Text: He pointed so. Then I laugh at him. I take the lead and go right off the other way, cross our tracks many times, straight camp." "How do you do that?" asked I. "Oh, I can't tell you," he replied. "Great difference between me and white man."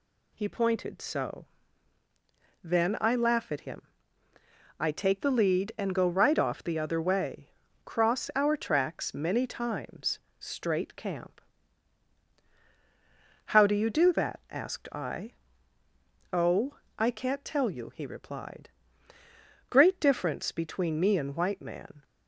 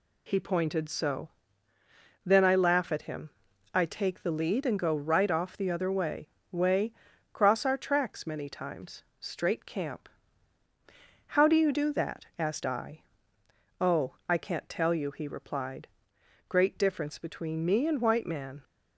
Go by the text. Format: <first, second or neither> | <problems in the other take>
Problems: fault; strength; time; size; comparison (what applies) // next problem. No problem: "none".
first | says "way" twice; at 6.5 s